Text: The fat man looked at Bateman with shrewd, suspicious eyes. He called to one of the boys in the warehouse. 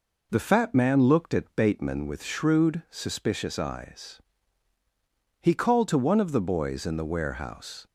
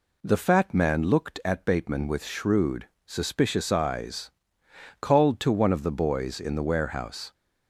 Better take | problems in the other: first | skips "He"; at 4.6 s

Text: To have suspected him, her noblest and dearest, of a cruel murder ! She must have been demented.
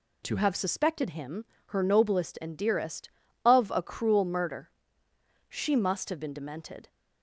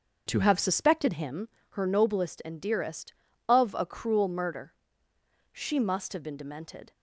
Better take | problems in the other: first | starts louder than the rest; until 1.5 s; 7 dB

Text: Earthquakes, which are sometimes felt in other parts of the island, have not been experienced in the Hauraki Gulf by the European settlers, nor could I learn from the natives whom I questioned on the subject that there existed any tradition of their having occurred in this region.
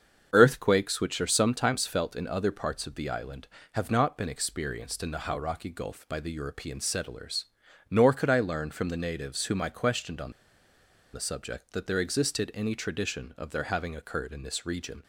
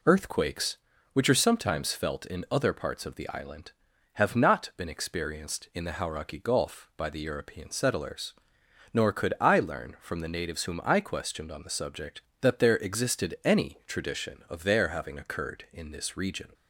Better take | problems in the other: second | starts louder than the rest; until 1.3 s; 7 dB // pauses between "on" and "the"; noticeable; at 10.3 s; 0.82 s long

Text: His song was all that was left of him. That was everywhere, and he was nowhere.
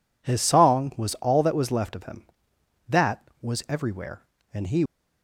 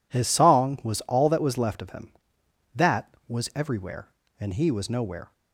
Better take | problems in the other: second | stops before "was nowhere"; at 4.8 s

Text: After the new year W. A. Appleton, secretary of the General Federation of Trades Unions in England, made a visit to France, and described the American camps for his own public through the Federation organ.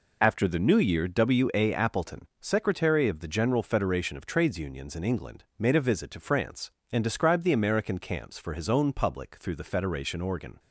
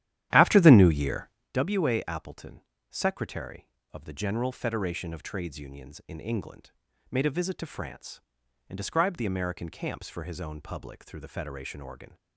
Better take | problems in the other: first | starts louder than the rest; strong; until 1.5 s; 12 dB // pauses between "year" and "W"; slight; at 1.2 s; 0.26 s long

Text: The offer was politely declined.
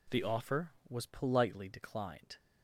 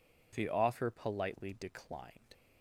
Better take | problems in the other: first | skips "was"; at 0.8 s

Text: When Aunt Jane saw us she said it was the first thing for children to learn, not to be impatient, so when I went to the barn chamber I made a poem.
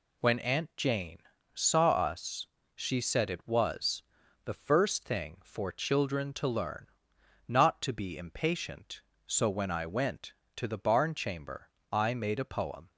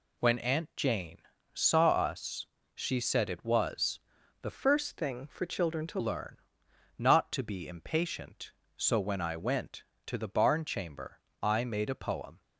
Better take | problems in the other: first | pauses between "Jane" and "saw"; slight; at 1.2 s; 0.32 s long; slight in the first // pauses between "us" and "she"; slight; at 2.4 s; 0.26 s long; slight in the first // pauses between "was" and "the"; at 3.9 s; 0.42 s long; also in the first // changes voice from "first" to "to"; from 4.5 to 6.0 s; 1.5 s long // pauses between "chamber" and "I"; slight; at 11.2 s; 0.20 s long; slight in the first

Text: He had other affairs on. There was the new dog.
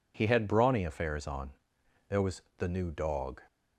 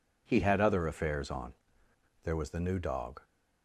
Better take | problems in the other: second | says "brawny" for "other"; at 0.4 s // pauses between "was" and "the"; slight; at 2.3 s; 0.18 s long

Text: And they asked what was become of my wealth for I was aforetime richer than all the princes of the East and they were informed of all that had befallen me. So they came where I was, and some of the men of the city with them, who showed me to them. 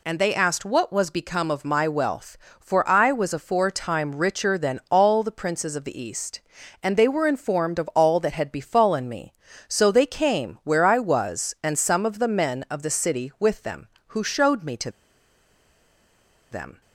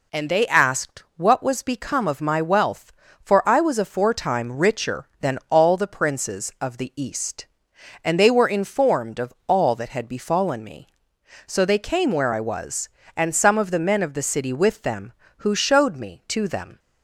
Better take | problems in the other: second | pauses between "to" and "them"; strong; at 14.9 s; 1.5 s long

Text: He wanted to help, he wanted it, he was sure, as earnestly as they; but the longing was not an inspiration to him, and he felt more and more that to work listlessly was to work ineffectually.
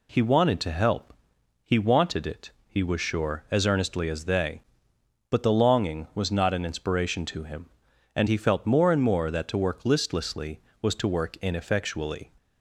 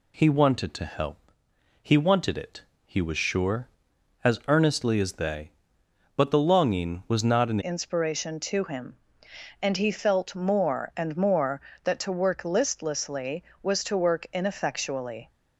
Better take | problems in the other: first | changes voice at "inspiration"; from 7.5 s on; 7.7 s long

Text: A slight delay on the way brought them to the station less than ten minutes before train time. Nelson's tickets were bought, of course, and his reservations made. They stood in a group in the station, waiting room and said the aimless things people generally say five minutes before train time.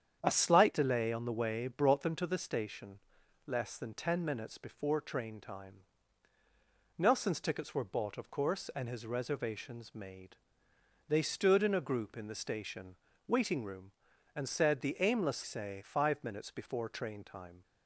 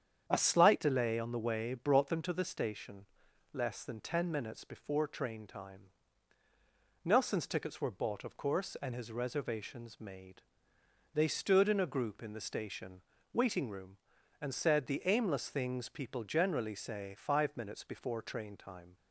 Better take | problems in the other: second | starts louder than the rest; strong; until 1.2 s; 8.5 dB; strong in the second // pauses between "station" and "less"; noticeable; at 2.9 s; 0.48 s long; noticeable in the second // skips "things people generally"; at 15.4 s

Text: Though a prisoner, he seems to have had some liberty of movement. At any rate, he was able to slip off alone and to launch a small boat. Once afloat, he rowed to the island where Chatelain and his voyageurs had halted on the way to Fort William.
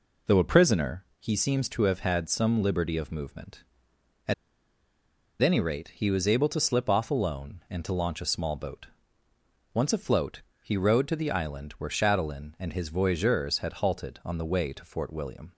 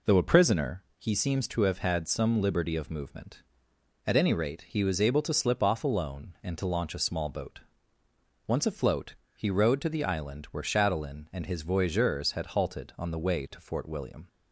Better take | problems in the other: second | pauses between "At" and "any"; at 4.3 s; 1.0 s long

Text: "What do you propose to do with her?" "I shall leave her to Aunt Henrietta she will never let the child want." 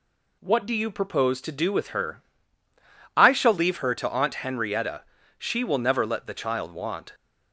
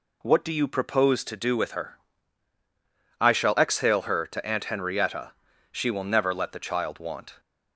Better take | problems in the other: first | says "exhale" for "leave"; at 3.5 s // pauses between "Henrietta" and "she"; at 5.3 s; 0.40 s long; slight in the first

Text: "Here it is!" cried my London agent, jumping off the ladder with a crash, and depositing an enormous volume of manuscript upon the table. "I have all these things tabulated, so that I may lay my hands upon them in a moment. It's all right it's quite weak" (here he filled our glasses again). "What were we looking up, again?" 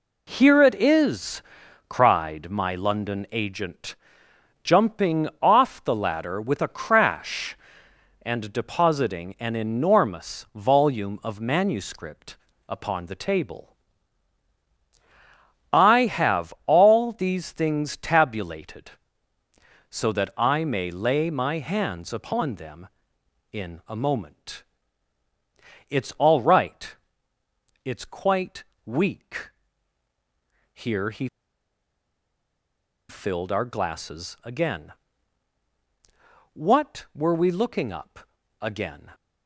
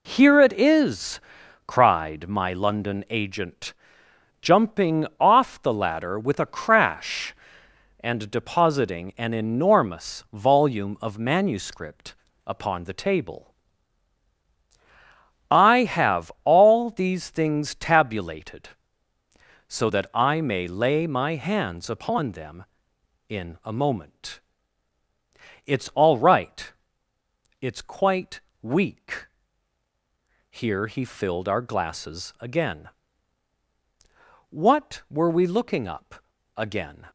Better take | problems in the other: second | pauses between "manuscript" and "upon"; slight; at 12.3 s; 0.32 s long; slight in the second // pauses between "right" and "it's"; noticeable; at 26.9 s; 0.92 s long; noticeable in the second // pauses between "quite" and "weak"; slight; at 28.6 s; 0.20 s long; slight in the second // pauses between "he" and "filled"; strong; at 31.2 s; 1.8 s long

